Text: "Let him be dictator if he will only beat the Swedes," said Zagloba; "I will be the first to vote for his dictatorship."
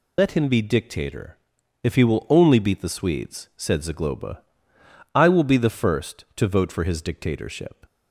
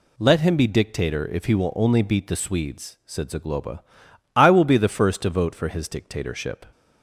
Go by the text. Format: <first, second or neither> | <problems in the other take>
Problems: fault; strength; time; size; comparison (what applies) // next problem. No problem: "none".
second | loses the start of "Let"; at 0.1 s; 85 ms // pauses between "dictator" and "if"; noticeable; at 1.3 s; 0.48 s long